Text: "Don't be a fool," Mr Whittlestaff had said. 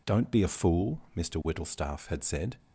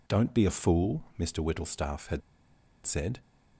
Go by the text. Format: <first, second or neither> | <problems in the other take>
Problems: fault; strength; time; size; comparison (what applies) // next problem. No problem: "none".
first | pauses between "had" and "said"; noticeable; at 2.2 s; 0.64 s long